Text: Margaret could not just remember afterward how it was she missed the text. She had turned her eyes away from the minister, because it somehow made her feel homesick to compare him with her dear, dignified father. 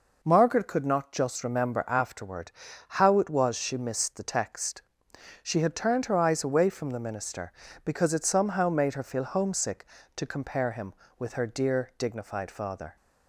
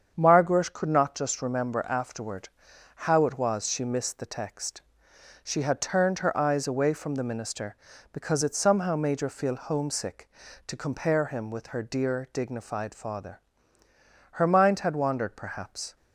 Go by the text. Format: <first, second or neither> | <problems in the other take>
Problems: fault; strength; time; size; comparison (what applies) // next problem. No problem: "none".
first | starts louder than the rest; strong; until 1.1 s; 7.5 dB // pauses between "afterward" and "how"; noticeable; at 2.4 s; 0.46 s long; noticeable in the first // goes on to say "Her mind had wandered perhaps"; from 14.3 s on; 1.6 s long